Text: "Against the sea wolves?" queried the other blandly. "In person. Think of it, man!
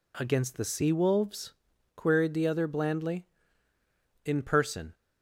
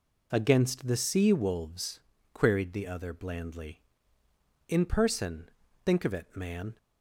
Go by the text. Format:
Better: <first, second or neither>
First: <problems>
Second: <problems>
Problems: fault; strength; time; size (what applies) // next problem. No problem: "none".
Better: second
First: stops before "Think of it man"; at 4.9 s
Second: none